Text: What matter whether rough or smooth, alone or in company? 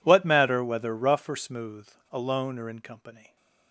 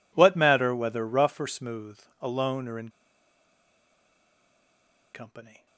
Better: first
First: none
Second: pauses between "in" and "company"; strong; at 2.8 s; 2.2 s long

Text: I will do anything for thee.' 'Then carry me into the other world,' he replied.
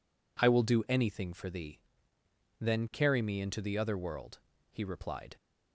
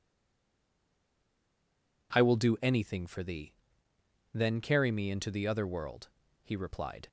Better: first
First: none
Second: stays silent before the first word; noticeable; until 2.1 s; 2.1 s long

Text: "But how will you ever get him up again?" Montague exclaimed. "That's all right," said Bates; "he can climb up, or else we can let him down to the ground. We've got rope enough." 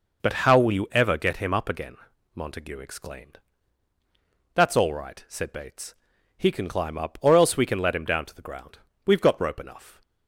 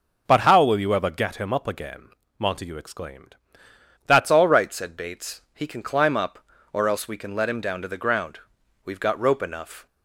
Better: first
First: none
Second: starts louder than the rest; noticeable; until 1.2 s; 6 dB // changes voice at "all"; from 4.3 s on; 5.5 s long

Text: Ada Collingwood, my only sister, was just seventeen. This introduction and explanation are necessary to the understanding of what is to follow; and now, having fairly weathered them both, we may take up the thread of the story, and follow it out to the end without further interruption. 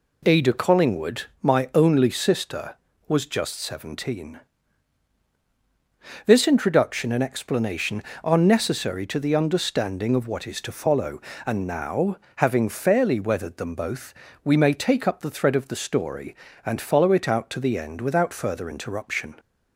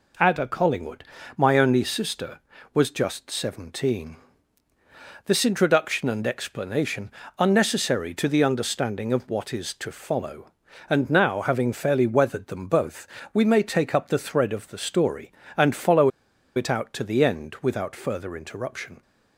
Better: first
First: none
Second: pauses between "follow" and "it"; noticeable; at 16.0 s; 0.46 s long

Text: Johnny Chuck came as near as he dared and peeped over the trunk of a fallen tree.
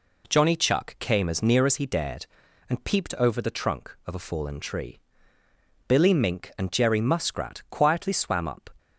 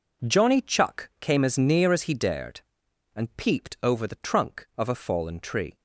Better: second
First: goes on to say "Billy Mink and Jerry Muskrat quietly swam up"; strong; from 5.8 s on; 2.8 s long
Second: none

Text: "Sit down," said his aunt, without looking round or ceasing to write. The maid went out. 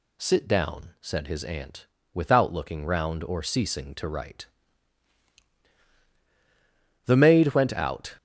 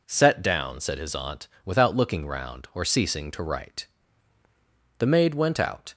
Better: first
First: none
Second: says "Set" for "Sit"; at 0.0 s

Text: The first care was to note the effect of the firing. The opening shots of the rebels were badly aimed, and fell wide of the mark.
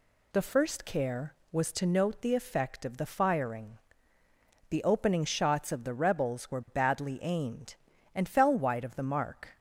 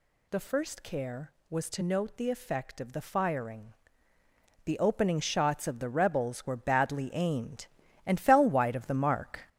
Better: first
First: none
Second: gets louder; throughout; 6.5 dB

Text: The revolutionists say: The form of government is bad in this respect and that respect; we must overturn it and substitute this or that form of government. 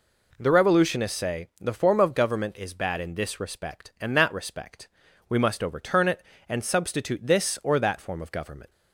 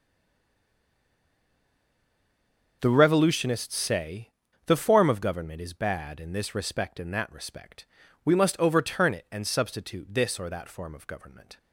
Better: first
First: none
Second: stays silent before the first word; strong; until 2.8 s; 2.8 s long // starts louder than the rest; until 3.8 s; 6 dB

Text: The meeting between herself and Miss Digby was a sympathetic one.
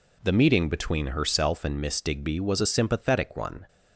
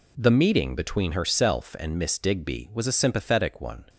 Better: neither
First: none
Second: none

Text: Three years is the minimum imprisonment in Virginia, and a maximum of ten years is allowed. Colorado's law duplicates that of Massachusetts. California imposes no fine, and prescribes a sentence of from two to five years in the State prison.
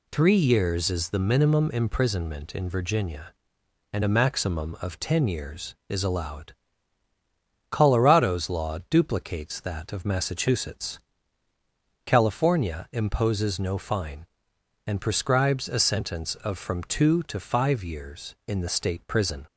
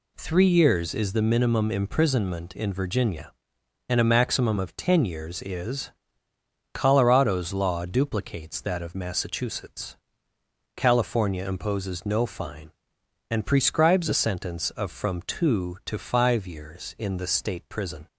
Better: first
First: none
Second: skips "allowed"; at 6.3 s

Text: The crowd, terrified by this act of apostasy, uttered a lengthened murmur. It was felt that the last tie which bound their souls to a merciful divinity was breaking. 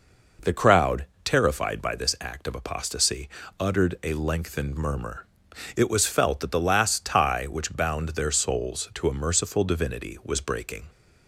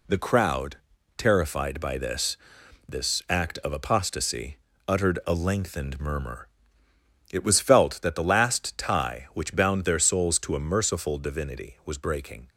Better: first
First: none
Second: says "this" twice; at 2.8 s

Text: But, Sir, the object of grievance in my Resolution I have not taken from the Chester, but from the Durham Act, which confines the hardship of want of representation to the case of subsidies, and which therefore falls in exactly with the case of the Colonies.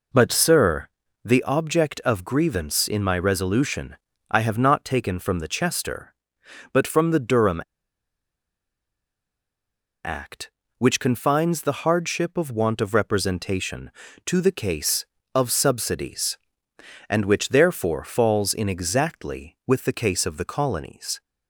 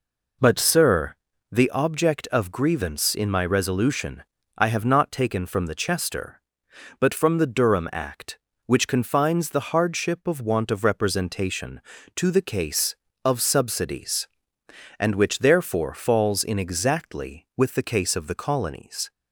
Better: second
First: pauses between "Resolution" and "I"; slight; at 3.9 s; 0.34 s long // pauses between "Durham" and "Act"; strong; at 7.6 s; 2.4 s long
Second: pauses between "Resolution" and "I"; slight; at 4.2 s; 0.34 s long

